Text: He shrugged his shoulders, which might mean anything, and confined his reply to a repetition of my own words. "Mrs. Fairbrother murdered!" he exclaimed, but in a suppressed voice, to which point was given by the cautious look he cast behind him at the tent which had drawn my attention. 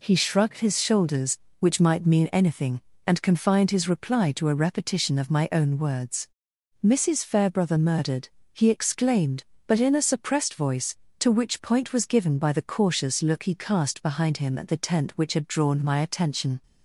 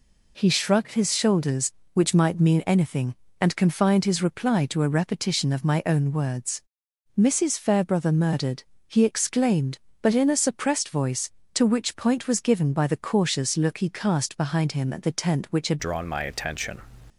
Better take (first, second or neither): first